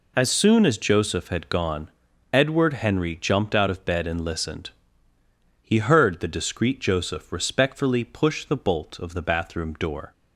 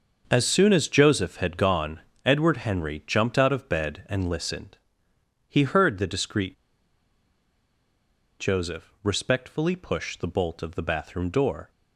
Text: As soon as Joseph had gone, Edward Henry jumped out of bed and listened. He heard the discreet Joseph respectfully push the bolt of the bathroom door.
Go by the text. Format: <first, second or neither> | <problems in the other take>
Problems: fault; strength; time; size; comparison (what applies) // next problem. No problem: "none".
first | starts louder than the rest; until 1.2 s; 6.5 dB // pauses between "discreet" and "Joseph"; strong; at 6.5 s; 1.8 s long